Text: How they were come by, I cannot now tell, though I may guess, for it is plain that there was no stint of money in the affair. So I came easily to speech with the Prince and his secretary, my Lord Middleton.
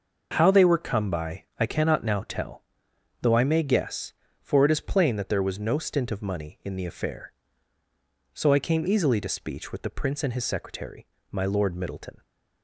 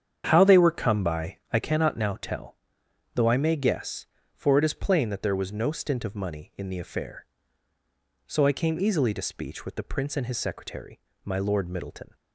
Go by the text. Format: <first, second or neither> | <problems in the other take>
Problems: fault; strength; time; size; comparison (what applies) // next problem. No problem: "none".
first | starts louder than the rest; strong; until 1.7 s; 8 dB